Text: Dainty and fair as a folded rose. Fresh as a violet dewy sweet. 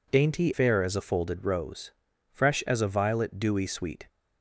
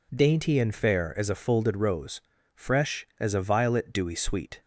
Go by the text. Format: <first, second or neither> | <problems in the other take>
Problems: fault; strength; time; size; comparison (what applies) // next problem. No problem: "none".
second | skips "and"; at 0.5 s